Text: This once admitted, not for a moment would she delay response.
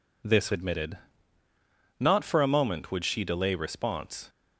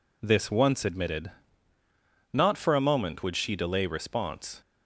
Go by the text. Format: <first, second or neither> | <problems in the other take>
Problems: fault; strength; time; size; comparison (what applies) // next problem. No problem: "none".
second | skips "once"; at 0.5 s